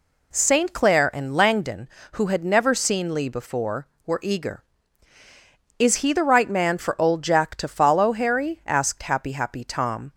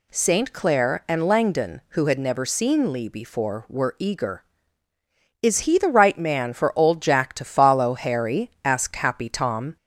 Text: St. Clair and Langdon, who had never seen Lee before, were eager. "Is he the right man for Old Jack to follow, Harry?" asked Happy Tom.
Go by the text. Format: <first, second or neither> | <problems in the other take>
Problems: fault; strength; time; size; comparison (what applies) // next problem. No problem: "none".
second | says "Happy" twice; at 9.3 s